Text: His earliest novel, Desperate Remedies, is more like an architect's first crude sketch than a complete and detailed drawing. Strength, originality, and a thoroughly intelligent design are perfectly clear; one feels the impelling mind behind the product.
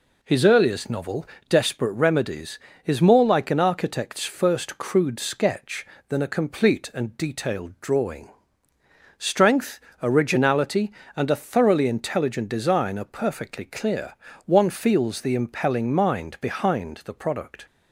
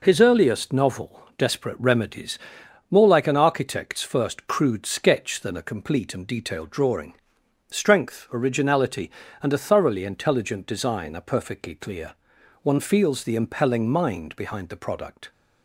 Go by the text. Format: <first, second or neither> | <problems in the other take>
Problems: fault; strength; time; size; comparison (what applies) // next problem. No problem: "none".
first | skips "is"; at 2.6 s